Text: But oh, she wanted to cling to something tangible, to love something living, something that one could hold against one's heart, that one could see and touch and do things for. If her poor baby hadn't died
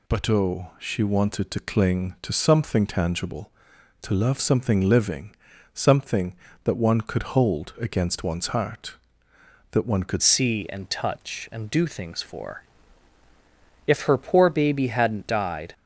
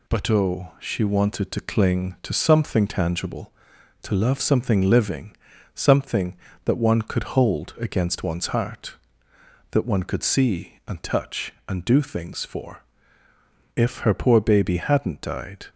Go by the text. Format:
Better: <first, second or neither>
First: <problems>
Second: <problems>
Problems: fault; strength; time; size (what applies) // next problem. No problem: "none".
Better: second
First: changes voice at "see"; from 10.2 s on; 5.5 s long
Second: none